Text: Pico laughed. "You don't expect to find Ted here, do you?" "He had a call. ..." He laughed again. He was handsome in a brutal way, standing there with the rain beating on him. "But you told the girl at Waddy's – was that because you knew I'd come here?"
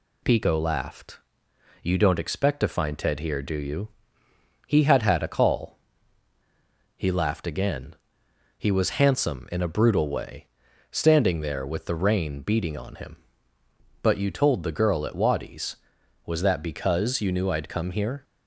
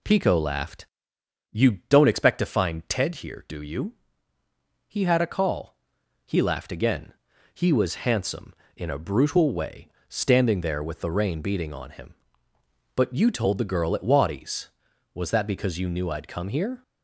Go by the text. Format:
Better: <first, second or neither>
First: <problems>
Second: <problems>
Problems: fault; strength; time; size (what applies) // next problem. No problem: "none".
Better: second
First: says "had" twice; at 5.0 s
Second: none